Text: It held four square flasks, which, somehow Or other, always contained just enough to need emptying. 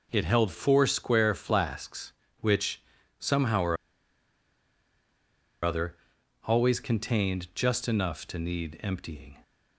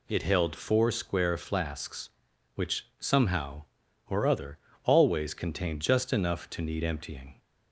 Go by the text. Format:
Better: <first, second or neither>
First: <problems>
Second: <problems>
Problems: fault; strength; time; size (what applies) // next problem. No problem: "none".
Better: second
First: pauses between "Or" and "other"; strong; at 3.7 s; 1.8 s long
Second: none